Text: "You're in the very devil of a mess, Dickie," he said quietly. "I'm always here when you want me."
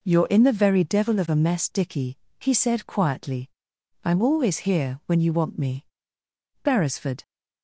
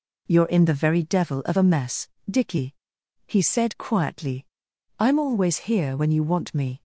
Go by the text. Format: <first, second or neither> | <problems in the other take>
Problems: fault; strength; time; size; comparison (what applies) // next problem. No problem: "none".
second | goes on to say "Beresford"; from 6.6 s on; 0.58 s long